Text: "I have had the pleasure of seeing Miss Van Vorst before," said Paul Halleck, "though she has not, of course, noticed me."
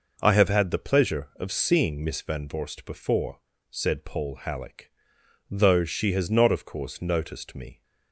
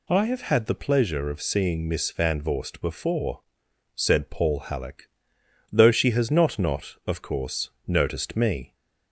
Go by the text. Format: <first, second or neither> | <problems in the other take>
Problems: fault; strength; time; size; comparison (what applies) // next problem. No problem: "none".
first | says "not" twice; at 6.5 s